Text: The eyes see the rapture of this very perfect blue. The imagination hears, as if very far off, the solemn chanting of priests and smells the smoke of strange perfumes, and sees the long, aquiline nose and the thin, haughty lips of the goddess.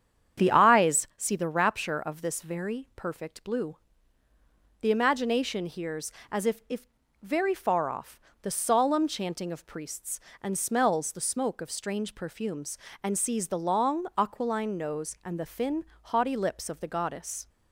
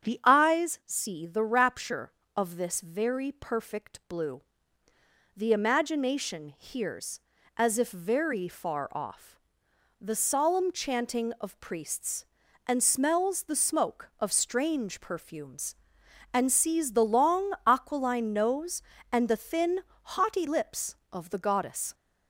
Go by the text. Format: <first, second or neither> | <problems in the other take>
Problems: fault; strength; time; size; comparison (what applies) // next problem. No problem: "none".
second | starts louder than the rest; strong; until 1.4 s; 8.5 dB; strong in the second // says "if" twice; at 6.6 s